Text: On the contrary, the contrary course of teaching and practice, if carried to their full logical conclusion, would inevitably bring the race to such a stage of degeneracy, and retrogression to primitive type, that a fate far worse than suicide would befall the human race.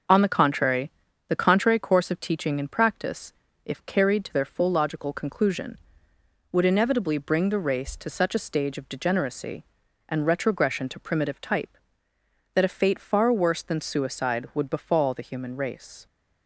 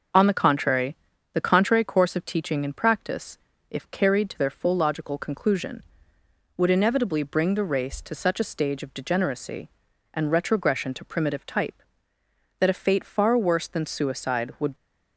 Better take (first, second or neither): first